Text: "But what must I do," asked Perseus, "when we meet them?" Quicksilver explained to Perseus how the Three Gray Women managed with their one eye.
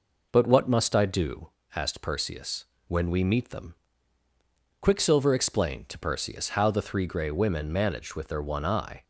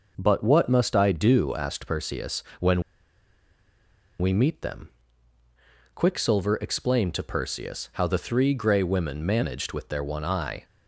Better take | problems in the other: first | pauses between "when" and "we"; strong; at 2.8 s; 1.3 s long

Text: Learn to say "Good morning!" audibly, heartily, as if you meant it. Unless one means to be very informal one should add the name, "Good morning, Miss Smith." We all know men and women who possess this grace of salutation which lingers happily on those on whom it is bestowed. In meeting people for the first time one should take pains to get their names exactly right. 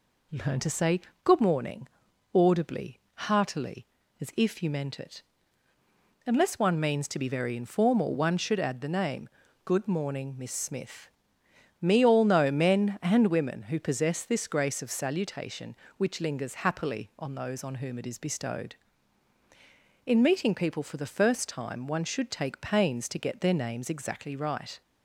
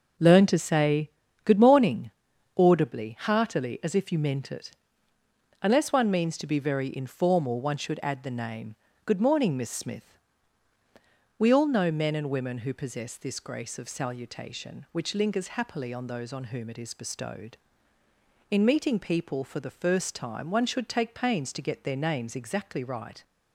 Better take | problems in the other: second | pauses between "say" and "Good"; slight; at 0.9 s; 0.24 s long; slight in the second // says "Me" for "We"; at 11.8 s

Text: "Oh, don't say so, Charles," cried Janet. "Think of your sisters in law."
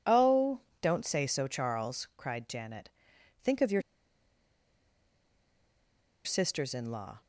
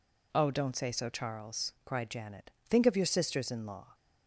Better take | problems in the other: second | pauses between "your" and "sisters"; strong; at 3.8 s; 2.4 s long

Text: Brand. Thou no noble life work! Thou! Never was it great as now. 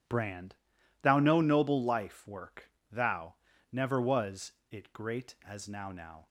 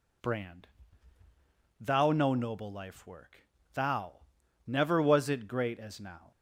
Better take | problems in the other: second | pauses between "was" and "it"; slight; at 4.5 s; 0.18 s long // says "now" twice; at 5.9 s

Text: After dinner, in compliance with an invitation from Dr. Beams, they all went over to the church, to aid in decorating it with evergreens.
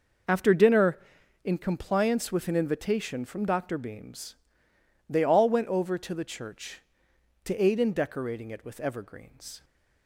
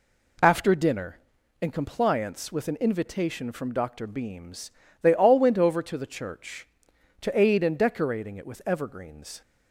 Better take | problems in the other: second | starts louder than the rest; noticeable; until 1.5 s; 6 dB

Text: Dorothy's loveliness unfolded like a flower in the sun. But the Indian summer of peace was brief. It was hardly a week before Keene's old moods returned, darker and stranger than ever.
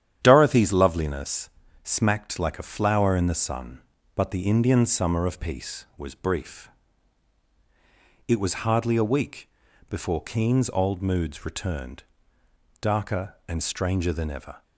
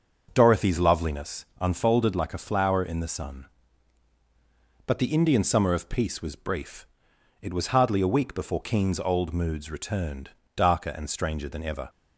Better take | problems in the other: second | starts louder than the rest; strong; until 1.2 s; 10 dB // says "smacked" for "unfolded"; at 1.8 s // pauses between "week" and "before"; at 9.4 s; 0.42 s long

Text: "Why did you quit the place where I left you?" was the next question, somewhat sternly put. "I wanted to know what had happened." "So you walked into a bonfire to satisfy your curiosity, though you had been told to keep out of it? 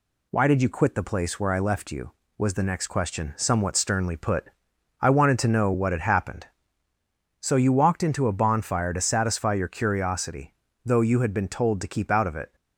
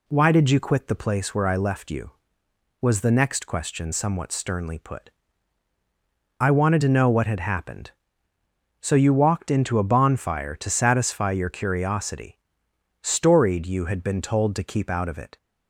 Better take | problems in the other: first | says "storied" for "though"; at 13.0 s

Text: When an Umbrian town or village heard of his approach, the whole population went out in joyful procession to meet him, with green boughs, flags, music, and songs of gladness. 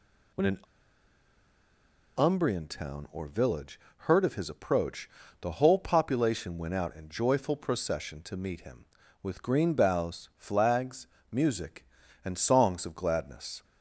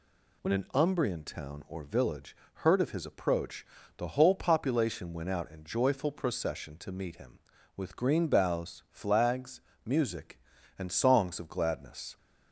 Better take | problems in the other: second | pauses between "an" and "Umbrian"; strong; at 0.5 s; 1.5 s long // pauses between "village" and "heard"; slight; at 3.7 s; 0.20 s long; slight in the second

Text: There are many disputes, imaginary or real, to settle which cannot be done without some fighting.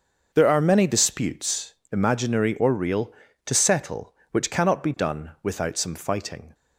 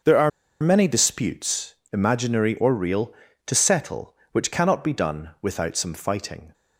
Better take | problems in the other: first | starts louder than the rest; until 1.3 s; 6.5 dB; also in the first // pauses between "are" and "many"; slight; at 0.2 s; 0.32 s long

